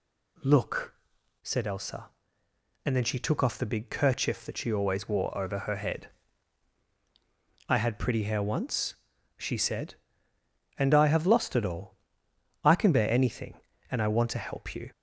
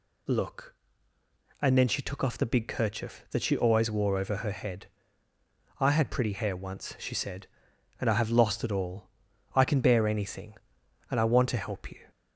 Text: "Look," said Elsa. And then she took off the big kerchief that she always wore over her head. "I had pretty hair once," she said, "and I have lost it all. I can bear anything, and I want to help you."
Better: first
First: none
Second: skips "said Elsa"; at 1.1 s

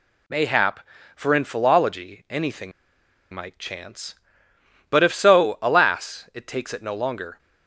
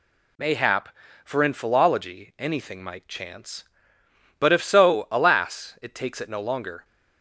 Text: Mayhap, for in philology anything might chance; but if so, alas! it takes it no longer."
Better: second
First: pauses between "anything" and "might"; noticeable; at 2.7 s; 0.62 s long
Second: none

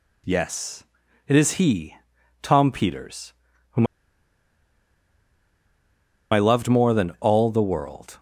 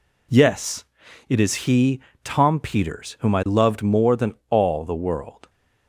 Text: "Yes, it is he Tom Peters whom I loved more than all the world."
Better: second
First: pauses between "he" and "Tom"; at 1.9 s; 0.44 s long // pauses between "Peters" and "whom"; at 3.3 s; 0.38 s long // pauses between "whom" and "I"; strong; at 3.8 s; 2.4 s long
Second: pauses between "he" and "Tom"; slight; at 1.9 s; 0.22 s long

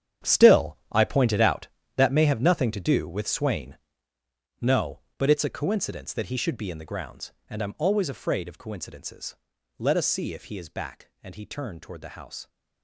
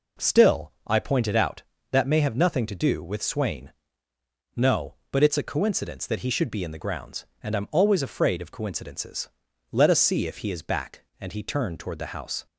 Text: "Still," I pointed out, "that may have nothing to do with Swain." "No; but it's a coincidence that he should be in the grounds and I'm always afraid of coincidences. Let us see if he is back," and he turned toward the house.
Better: second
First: gets quieter; strong; throughout; 14.5 dB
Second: none

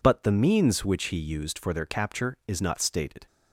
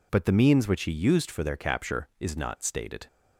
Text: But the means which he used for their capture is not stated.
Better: neither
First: none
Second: none

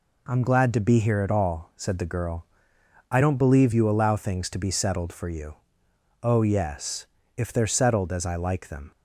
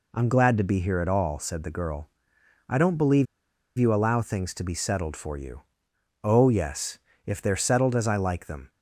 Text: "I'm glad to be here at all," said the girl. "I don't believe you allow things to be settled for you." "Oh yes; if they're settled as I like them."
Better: first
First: none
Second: pauses between "believe" and "you"; noticeable; at 3.2 s; 0.53 s long

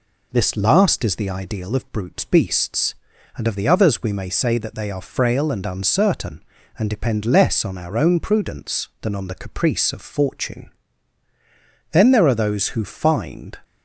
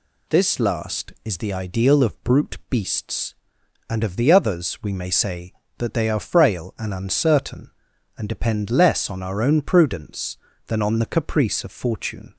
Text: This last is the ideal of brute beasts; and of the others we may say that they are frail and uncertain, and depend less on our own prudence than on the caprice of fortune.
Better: second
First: goes on to say "Then there are those who find"; from 11.9 s on; 1.6 s long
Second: none

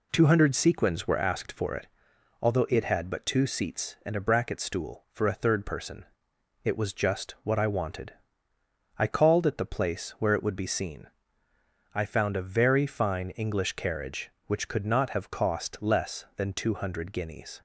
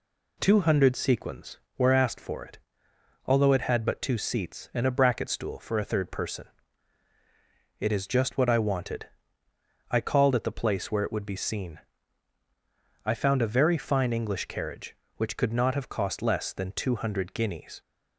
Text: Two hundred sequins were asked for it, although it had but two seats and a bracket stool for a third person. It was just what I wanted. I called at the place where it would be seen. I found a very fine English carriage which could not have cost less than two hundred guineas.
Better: first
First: none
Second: says "is" for "was"; at 7.9 s

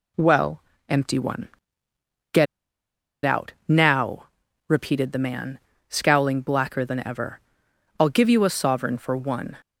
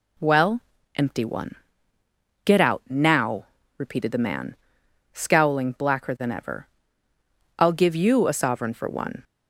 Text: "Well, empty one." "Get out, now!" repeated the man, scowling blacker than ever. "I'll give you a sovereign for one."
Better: second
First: pauses between "Get" and "out"; noticeable; at 2.4 s; 0.79 s long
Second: none

